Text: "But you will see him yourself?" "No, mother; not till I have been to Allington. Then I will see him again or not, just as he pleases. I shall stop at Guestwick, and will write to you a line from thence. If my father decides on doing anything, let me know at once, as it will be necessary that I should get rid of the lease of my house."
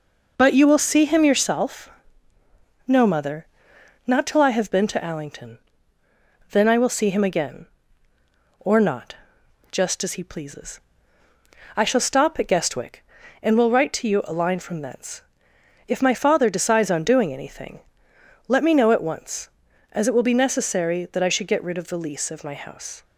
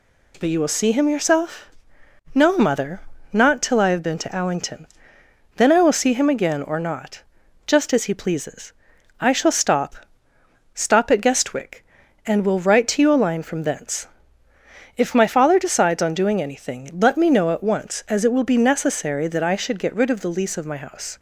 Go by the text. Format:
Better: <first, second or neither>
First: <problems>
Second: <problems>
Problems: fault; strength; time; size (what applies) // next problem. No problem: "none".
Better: first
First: none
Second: says "stop" twice; at 10.7 s